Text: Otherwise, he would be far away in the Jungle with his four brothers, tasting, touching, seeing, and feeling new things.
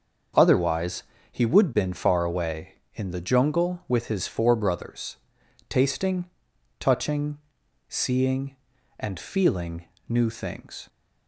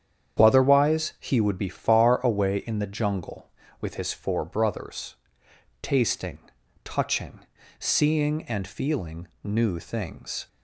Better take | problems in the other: second | starts louder than the rest; until 1.6 s; 6.5 dB; strong in the second // says "been" for "be"; at 1.7 s // pauses between "feeling" and "new"; slight; at 9.8 s; 0.22 s long; slight in the second

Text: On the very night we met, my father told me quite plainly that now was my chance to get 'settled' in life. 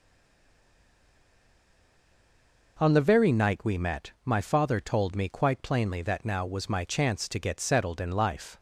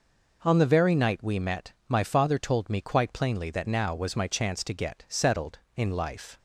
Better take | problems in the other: second | stays silent before the first word; strong; until 2.7 s; 2.7 s long

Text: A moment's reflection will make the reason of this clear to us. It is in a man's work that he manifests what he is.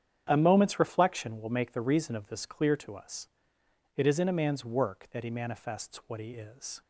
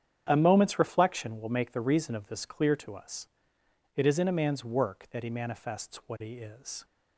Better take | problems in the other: neither | starts louder than the rest; strong; the same in both

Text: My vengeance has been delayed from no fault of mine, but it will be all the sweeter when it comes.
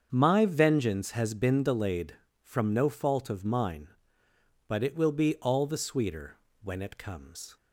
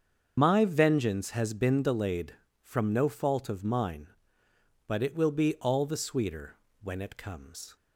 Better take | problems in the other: first | loses the start of "My"; at 0.3 s; 60 ms // starts louder than the rest; until 1.3 s; 7 dB; strong in the first // pauses between "sweeter" and "when"; slight; at 6.5 s; 0.28 s long; slight in the first

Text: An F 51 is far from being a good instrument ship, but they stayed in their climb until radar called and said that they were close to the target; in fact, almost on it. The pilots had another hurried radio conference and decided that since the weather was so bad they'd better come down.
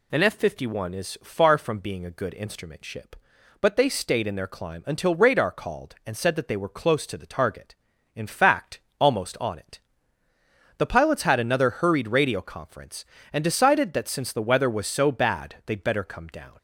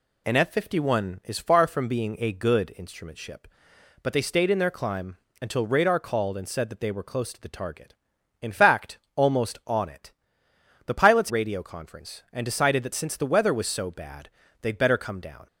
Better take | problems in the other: first | pauses between "climb" and "until"; slight; at 5.1 s; 0.26 s long // skips "had another hurried"; at 11.2 s // pauses between "bad" and "they'd"; slight; at 14.2 s; 0.32 s long

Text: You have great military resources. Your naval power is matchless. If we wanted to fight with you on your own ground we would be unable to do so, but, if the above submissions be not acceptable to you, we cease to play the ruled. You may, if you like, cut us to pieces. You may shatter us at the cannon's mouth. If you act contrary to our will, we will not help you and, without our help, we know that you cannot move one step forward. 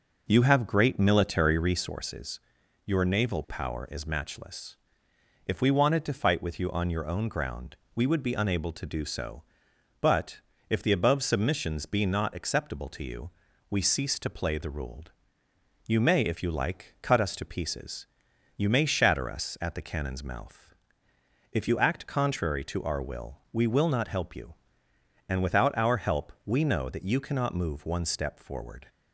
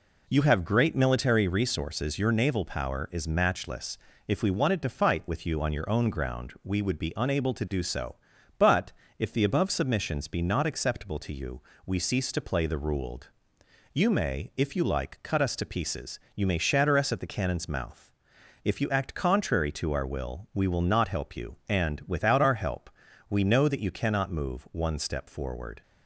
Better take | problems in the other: second | starts louder than the rest; noticeable; until 2.1 s; 5.5 dB // pauses between "ground" and "we"; slight; at 7.7 s; 0.18 s long

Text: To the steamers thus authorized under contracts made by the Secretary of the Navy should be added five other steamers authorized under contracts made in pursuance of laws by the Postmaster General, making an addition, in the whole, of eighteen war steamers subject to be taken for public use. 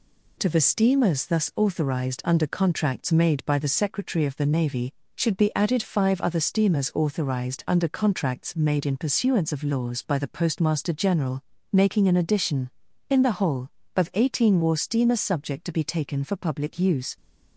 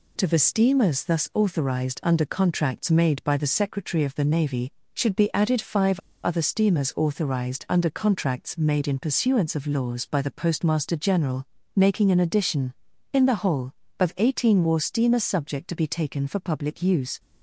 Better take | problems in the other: first | pauses between "five" and "other"; slight; at 5.9 s; 0.24 s long

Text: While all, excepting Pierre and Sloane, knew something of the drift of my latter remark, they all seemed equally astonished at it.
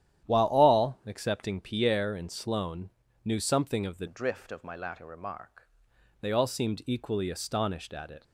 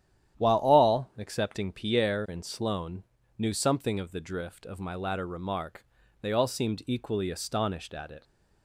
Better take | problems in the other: second | starts louder than the rest; strong; until 1.3 s; 11 dB; strong in the second // changes voice from "drift" to "remark"; from 4.0 to 5.6 s; 1.6 s long

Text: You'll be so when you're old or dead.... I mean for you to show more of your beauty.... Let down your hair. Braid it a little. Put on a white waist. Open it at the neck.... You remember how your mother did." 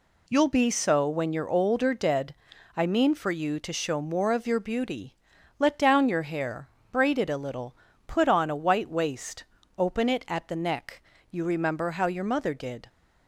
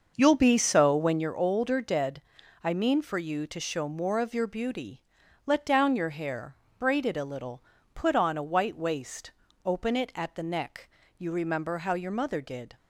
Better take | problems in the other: first | starts louder than the rest; noticeable; until 1.3 s; 6 dB

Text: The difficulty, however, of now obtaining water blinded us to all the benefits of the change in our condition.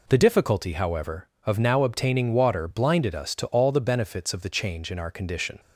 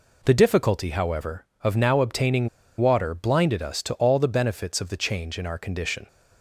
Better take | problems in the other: first | pauses between "obtaining" and "water"; slight; at 2.4 s; 0.32 s long

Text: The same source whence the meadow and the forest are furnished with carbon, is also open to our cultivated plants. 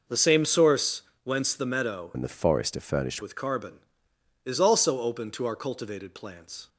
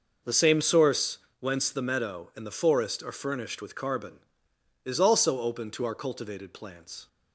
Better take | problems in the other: second | pauses between "source" and "whence"; slight; at 1.0 s; 0.22 s long; slight in the second // changes voice from "and" to "furnished"; from 2.1 to 3.2 s; 1.1 s long

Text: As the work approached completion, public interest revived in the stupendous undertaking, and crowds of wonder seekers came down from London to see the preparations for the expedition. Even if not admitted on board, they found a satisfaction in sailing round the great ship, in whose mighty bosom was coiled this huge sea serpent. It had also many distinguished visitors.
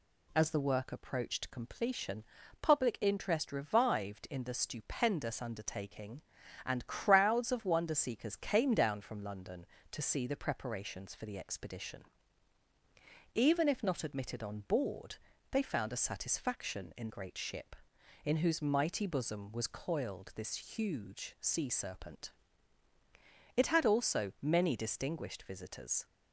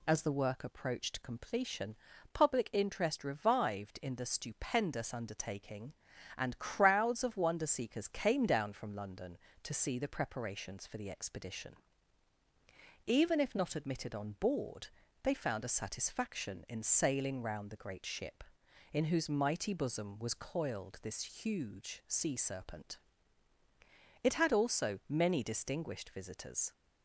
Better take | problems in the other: second | skips "sailing round the"; at 17.0 s

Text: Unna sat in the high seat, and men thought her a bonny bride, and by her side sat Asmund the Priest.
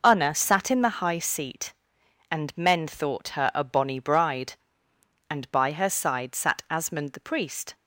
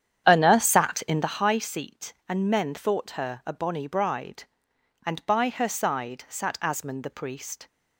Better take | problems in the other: first | starts louder than the rest; strong; until 1.5 s; 9 dB

